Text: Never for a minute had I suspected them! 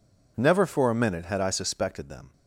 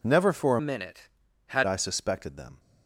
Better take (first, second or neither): first